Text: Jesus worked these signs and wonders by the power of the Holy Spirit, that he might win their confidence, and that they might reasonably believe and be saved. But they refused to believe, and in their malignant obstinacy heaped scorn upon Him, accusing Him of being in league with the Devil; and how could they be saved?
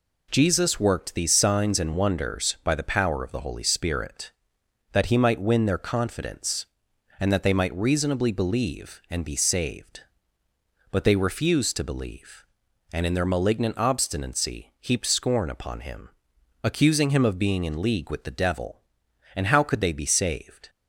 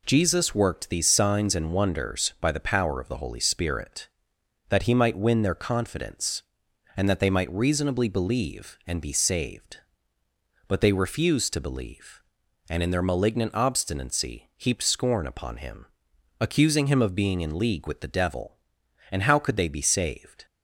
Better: neither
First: none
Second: none

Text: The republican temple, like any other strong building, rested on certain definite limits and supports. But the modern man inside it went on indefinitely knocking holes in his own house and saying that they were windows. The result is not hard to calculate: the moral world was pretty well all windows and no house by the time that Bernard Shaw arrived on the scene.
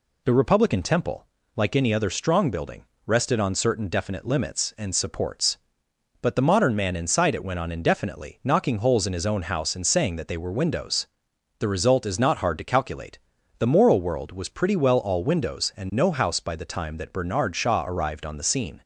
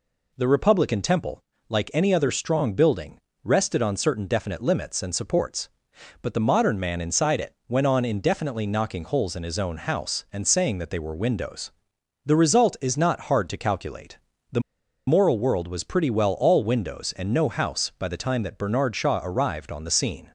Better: first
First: none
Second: pauses between "the" and "moral"; noticeable; at 14.6 s; 0.48 s long

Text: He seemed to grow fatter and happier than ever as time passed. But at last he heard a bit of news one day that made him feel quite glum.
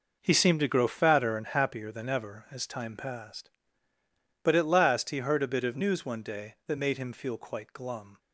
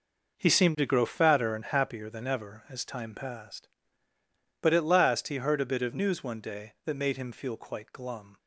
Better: neither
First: none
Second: none

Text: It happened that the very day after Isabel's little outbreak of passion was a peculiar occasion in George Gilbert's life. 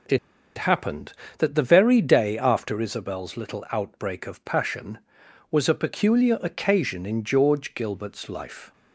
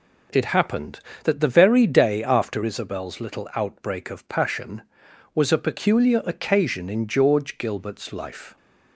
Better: second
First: pauses between "It" and "happened"; at 0.1 s; 0.39 s long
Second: none

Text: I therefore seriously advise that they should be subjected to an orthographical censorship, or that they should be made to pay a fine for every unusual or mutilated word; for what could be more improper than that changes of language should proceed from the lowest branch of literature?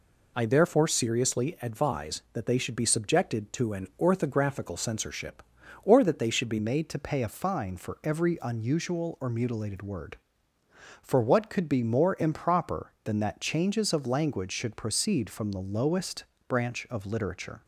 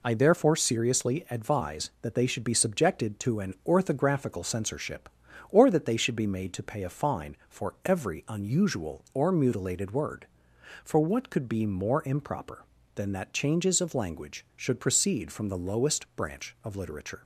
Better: second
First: changes voice at "made"; from 6.5 s on; 11.1 s long // pauses between "lowest" and "branch"; slight; at 16.2 s; 0.22 s long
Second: none

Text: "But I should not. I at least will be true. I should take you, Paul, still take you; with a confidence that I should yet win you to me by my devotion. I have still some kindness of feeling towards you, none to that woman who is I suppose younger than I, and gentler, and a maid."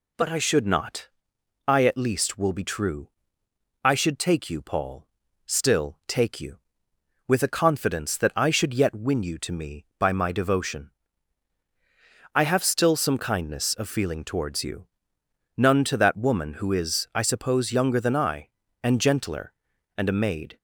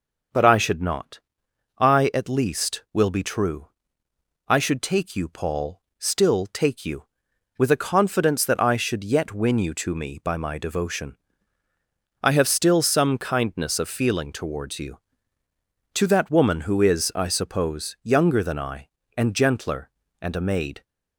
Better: first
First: none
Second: skips "none"; at 15.4 s

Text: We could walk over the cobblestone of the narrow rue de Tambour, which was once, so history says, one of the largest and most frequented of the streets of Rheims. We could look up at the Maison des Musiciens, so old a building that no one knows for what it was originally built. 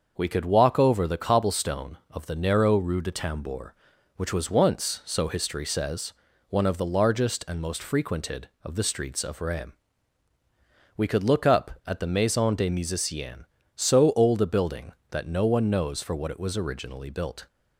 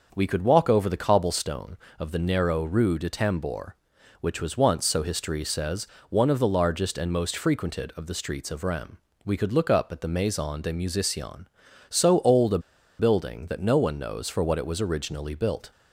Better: first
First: starts louder than the rest; until 1.2 s; 6.5 dB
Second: starts louder than the rest; until 1.1 s; 6 dB // pauses between "a" and "building"; at 12.5 s; 0.40 s long

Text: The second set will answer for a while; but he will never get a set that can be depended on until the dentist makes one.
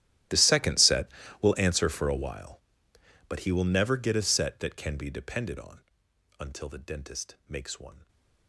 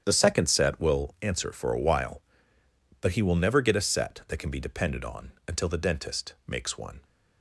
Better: second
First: gets quieter; strong; throughout; 23.5 dB // starts louder than the rest; strong; until 1.6 s; 13.5 dB // pauses between "on" and "until"; noticeable; at 5.7 s; 0.60 s long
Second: starts louder than the rest; strong; until 1.0 s; 8.5 dB // pauses between "on" and "until"; slight; at 5.3 s; 0.16 s long

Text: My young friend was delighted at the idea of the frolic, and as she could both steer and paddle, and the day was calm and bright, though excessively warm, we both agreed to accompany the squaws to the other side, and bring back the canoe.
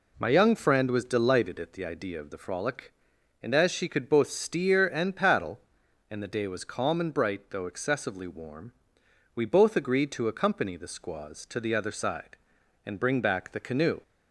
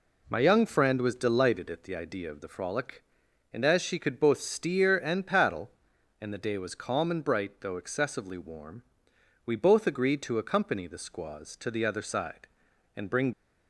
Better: first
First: none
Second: stops before "back the canoe"; at 13.3 s

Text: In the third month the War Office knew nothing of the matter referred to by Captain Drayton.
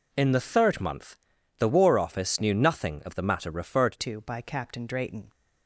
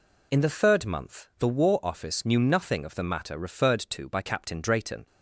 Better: second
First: pauses between "month" and "the"; at 1.1 s; 0.42 s long // changes voice at "to"; from 4.0 s on; 1.3 s long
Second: none

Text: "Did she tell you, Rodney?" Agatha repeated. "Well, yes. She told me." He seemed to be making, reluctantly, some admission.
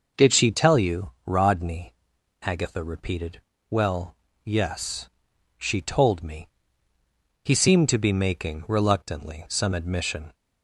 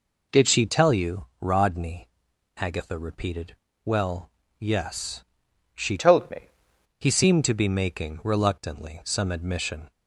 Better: first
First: none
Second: changes voice from "told" to "me"; from 5.9 to 6.4 s; 0.5 s long

